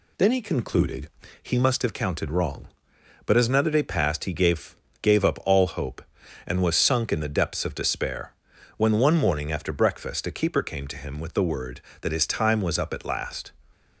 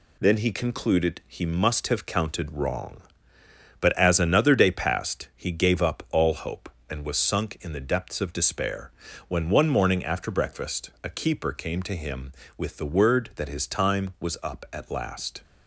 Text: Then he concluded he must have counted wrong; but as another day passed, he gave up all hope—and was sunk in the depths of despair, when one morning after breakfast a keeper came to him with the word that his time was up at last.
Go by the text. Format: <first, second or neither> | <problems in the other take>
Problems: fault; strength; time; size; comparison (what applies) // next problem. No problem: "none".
second | pauses between "concluded" and "he"; slight; at 1.0 s; 0.34 s long // says "gave" twice; at 5.0 s